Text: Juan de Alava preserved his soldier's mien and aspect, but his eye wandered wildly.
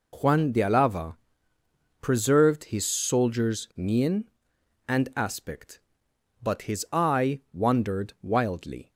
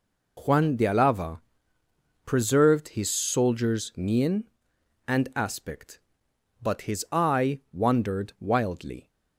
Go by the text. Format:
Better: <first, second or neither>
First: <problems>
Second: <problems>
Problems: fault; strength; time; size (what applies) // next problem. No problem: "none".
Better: neither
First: pauses between "Alava" and "preserved"; noticeable; at 1.1 s; 0.84 s long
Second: pauses between "Alava" and "preserved"; noticeable; at 1.4 s; 0.84 s long